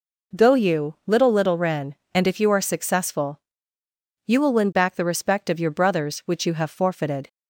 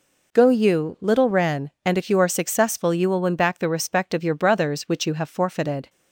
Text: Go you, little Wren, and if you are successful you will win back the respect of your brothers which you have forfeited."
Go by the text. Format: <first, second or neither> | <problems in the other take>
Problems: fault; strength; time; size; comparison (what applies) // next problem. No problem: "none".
second | says "little" twice; at 1.3 s // pauses between "successful" and "you"; noticeable; at 3.3 s; 0.88 s long